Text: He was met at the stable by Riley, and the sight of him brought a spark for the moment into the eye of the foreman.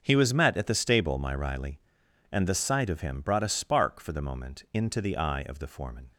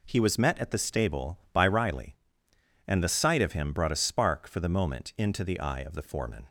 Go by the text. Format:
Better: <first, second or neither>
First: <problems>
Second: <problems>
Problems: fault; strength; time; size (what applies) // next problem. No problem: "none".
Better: second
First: starts louder than the rest; until 1.0 s; 6.5 dB // says "my" for "by"; at 1.1 s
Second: none